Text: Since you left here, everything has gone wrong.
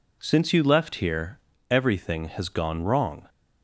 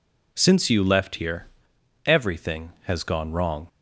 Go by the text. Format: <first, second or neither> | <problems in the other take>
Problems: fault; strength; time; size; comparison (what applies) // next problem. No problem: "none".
neither | none